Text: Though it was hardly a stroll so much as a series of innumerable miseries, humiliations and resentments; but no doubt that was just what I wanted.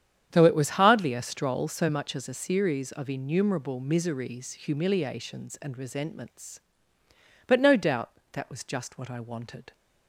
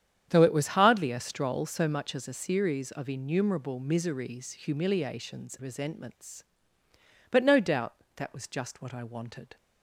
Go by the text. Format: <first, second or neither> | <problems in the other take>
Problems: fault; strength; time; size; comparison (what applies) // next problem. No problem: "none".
first | starts louder than the rest; strong; until 1.3 s; 9 dB; strong in the first // skips "and"; at 5.5 s